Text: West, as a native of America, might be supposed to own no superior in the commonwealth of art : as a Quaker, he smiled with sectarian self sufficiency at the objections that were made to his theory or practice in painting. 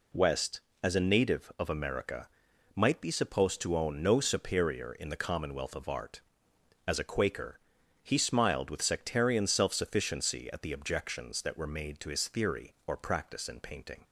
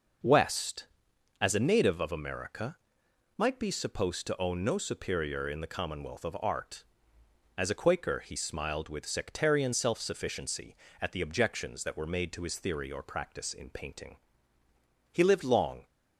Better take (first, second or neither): first